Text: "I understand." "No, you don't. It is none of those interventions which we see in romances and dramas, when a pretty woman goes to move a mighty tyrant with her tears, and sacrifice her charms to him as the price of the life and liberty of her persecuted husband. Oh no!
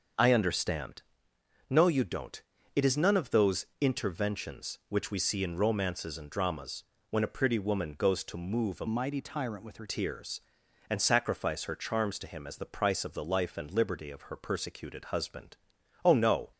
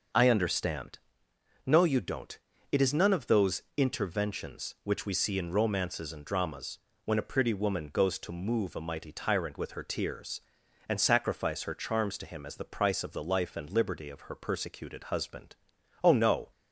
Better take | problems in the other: second | starts louder than the rest; until 1.8 s; 6.5 dB; noticeable in the second // pauses between "those" and "interventions"; slight; at 3.6 s; 0.16 s long; slight in the second // changes voice from "mighty" to "her"; from 8.8 to 9.8 s; 1.0 s long

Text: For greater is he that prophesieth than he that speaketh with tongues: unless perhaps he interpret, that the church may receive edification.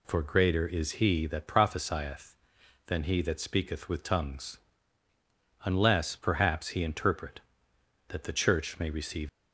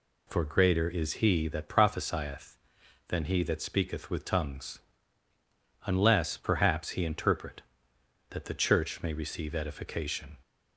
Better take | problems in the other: second | stops before "edification"; at 9.2 s

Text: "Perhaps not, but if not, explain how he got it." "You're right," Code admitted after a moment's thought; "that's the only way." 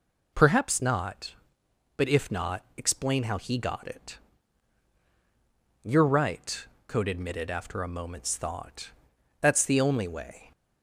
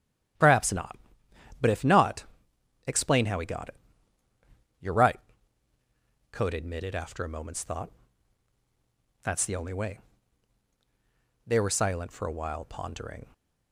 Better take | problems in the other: first | starts louder than the rest; strong; until 2.0 s; 11 dB // goes on to say "They were silent for a while pondering"; strong; from 11.4 s on; 1.8 s long

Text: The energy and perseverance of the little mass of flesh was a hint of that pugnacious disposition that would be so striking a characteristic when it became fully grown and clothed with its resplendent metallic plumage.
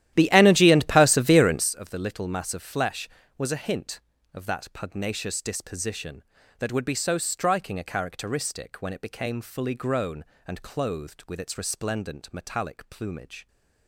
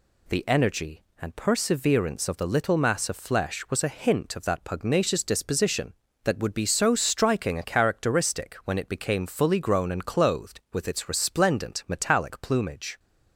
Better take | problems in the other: second | starts louder than the rest; strong; until 1.7 s; 12.5 dB

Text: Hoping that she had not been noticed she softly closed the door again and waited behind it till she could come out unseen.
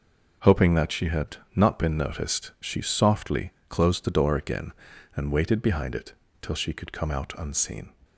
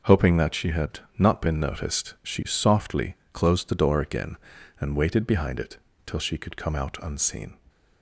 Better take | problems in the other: neither | pauses between "had" and "not"; slight; the same in both // pauses between "softly" and "closed"; slight; the same in both // pauses between "it" and "till"; slight; the same in both

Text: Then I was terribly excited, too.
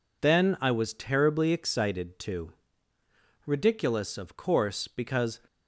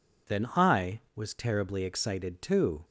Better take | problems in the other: second | goes on to say "Ridiculous of course because"; strong; from 3.4 s on; 1.9 s long

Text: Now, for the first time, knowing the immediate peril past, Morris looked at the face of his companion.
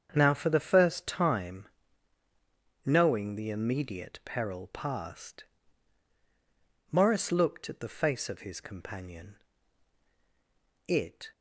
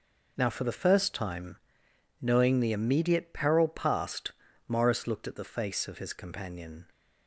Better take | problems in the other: second | starts louder than the rest; strong; until 1.1 s; 7 dB // goes on to say "It"; slight; from 10.8 s on; 0.42 s long

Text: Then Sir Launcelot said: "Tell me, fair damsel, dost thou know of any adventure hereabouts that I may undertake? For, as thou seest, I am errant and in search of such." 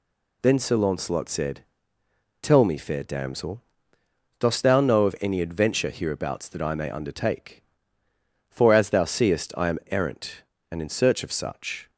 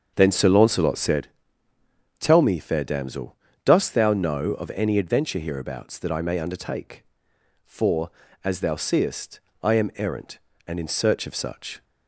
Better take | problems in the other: first | starts louder than the rest; until 1.3 s; 7 dB

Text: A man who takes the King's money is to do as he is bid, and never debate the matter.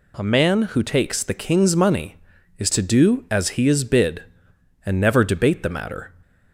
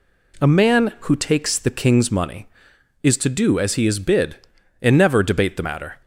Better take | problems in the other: neither | none

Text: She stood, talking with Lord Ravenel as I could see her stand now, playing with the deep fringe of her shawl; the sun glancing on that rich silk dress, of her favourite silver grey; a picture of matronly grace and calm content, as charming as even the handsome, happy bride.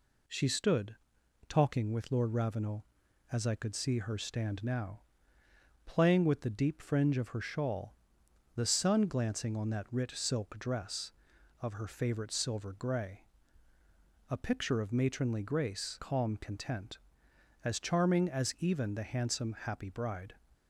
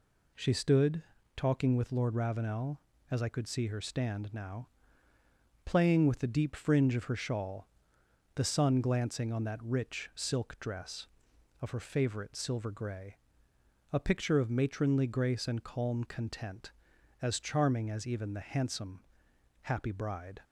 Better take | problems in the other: second | skips "and"; at 15.9 s

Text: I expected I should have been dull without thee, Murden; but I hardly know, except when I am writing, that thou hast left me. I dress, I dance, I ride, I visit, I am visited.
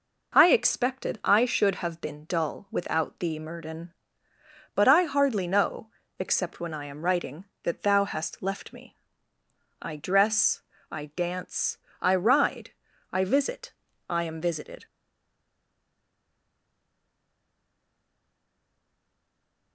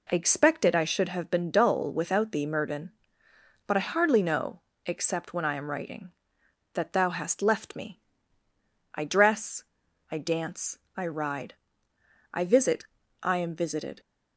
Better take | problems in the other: second | stays silent after the last word; strong; from 14.8 s on; 4.9 s long

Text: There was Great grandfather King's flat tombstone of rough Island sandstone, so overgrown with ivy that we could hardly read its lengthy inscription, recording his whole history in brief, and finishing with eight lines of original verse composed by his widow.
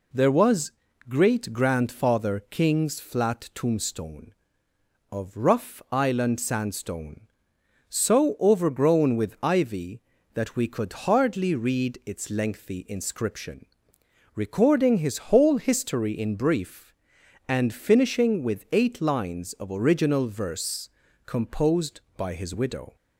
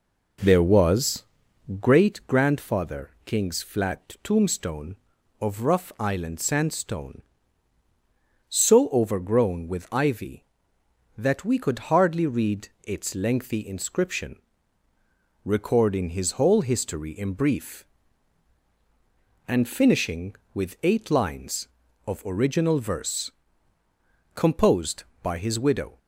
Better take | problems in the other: first | starts louder than the rest; noticeable; until 1.9 s; 5 dB // pauses between "was" and "Great"; noticeable; at 1.2 s; 0.56 s long; slight in the first // pauses between "read" and "its"; slight; at 12.6 s; 0.18 s long // pauses between "verse" and "composed"; at 23.3 s; 1.0 s long; slight in the first

